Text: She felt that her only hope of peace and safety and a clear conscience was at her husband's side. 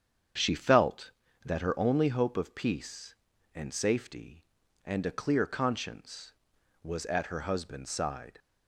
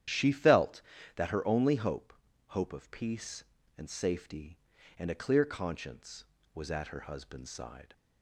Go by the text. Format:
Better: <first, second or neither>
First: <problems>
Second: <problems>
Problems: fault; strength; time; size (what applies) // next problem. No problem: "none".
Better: first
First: starts louder than the rest; strong; until 1.7 s; 8 dB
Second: starts louder than the rest; strong; until 1.4 s; 10.5 dB // says "hope" twice; at 2.5 s